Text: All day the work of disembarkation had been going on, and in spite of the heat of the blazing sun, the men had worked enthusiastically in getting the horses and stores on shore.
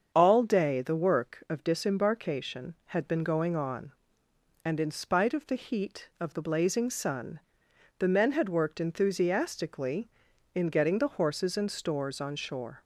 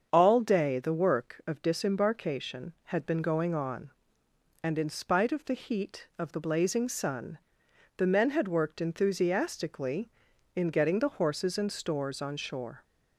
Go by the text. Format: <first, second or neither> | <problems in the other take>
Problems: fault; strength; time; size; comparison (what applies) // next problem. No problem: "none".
neither | starts louder than the rest; the same in both